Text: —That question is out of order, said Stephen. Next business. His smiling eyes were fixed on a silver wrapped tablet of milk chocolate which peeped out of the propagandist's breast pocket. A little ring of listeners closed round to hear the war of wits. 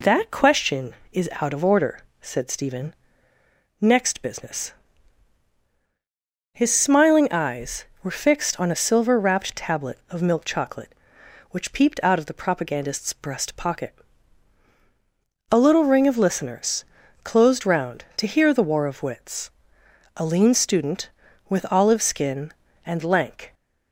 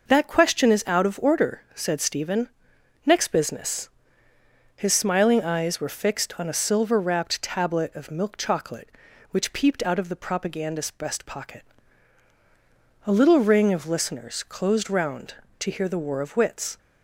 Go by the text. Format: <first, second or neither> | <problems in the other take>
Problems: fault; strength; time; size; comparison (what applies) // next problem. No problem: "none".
second | pauses between "listeners" and "closed"; at 16.8 s; 0.38 s long // goes on to say "A lean student with olive skin and lank"; strong; from 20.1 s on; 3.3 s long